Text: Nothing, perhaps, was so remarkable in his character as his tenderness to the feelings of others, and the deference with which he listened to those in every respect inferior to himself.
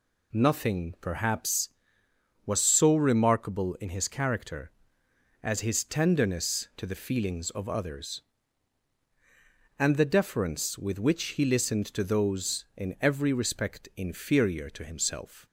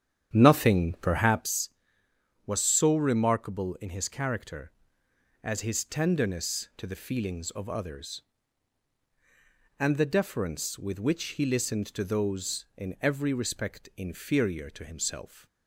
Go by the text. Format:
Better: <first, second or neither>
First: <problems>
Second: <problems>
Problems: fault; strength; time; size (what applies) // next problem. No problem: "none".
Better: first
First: none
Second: starts louder than the rest; strong; until 1.5 s; 9.5 dB